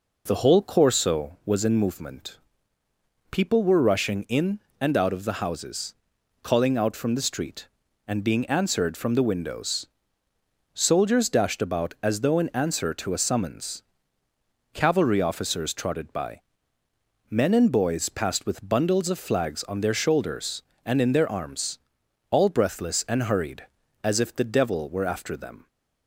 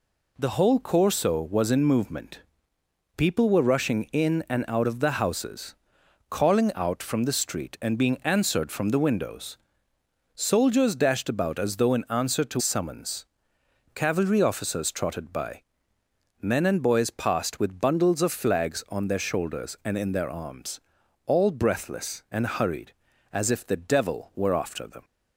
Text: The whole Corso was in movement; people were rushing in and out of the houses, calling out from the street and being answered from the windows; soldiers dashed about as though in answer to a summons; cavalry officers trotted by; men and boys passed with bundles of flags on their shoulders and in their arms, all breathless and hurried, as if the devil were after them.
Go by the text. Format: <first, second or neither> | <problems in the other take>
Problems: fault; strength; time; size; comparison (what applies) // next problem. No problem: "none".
first | skips "a"; at 12.5 s